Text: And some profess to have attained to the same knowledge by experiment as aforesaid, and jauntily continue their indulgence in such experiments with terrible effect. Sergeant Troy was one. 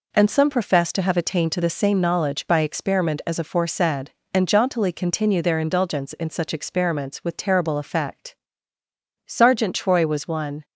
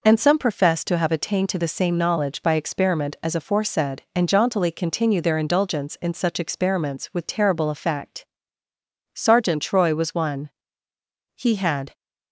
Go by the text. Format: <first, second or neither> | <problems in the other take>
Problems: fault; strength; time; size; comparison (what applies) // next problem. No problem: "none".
first | goes on to say "He had"; from 11.3 s on; 0.58 s long